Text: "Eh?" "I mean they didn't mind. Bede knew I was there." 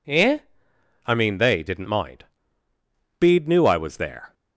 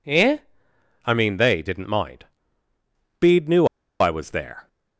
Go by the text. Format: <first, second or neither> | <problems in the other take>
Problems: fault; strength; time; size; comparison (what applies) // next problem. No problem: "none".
first | pauses between "knew" and "I"; slight; at 3.6 s; 0.33 s long